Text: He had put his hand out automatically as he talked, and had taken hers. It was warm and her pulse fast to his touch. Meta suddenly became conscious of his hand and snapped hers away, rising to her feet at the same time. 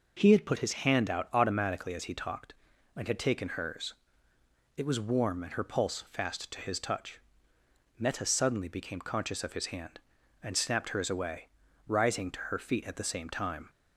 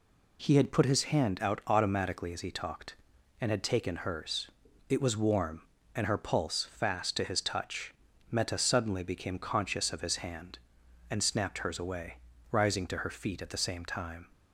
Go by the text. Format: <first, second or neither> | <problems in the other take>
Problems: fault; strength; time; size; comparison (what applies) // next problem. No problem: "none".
neither | none